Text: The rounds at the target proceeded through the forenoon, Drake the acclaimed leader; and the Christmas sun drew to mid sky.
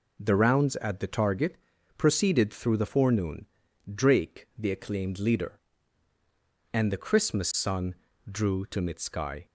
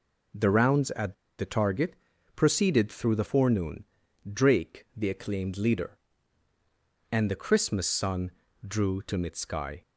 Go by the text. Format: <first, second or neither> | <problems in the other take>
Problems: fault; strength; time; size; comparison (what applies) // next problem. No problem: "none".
first | pauses between "at" and "the"; slight; at 1.1 s; 0.24 s long // pauses between "target" and "proceeded"; at 1.9 s; 0.42 s long; also in the first // pauses between "sun" and "drew"; slight; at 8.2 s; 0.36 s long; slight in the first